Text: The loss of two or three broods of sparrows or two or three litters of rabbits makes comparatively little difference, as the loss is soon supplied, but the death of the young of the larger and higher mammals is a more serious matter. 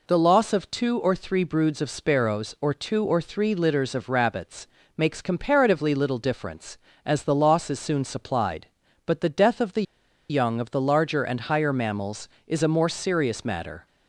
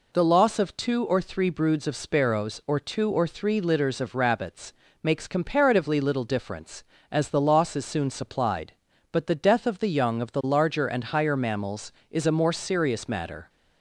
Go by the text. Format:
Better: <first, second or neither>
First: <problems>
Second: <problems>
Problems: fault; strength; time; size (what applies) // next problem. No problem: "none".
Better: second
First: pauses between "rabbits" and "makes"; slight; at 4.6 s; 0.28 s long // pauses between "the" and "young"; noticeable; at 9.8 s; 0.47 s long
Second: pauses between "rabbits" and "makes"; slight; at 4.7 s; 0.28 s long